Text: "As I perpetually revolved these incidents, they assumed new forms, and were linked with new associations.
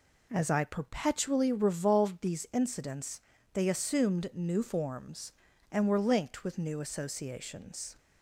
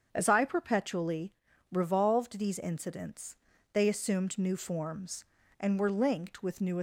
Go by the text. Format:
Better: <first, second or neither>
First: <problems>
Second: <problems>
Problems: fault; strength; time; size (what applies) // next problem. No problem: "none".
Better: first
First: none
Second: starts louder than the rest; until 1.1 s; 7 dB // pauses between "perpetually" and "revolved"; at 1.3 s; 0.38 s long // stops before "associations"; at 6.7 s